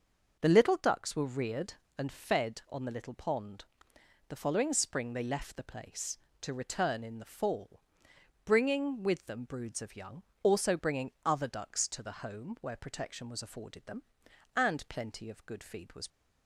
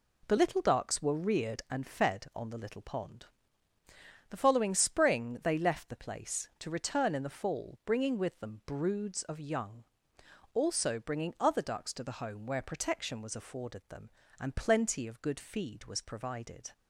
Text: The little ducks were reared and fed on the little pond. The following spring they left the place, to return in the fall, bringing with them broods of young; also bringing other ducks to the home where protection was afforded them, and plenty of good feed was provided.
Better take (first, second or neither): second